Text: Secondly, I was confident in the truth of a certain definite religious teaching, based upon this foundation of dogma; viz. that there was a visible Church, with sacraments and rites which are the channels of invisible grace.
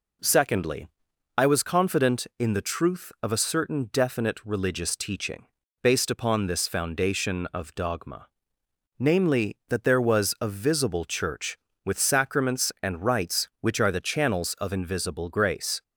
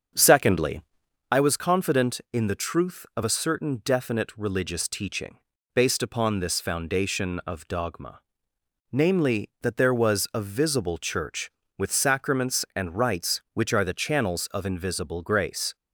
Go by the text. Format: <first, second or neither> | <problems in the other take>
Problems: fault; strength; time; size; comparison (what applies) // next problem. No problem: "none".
first | starts louder than the rest; until 1.3 s; 6.5 dB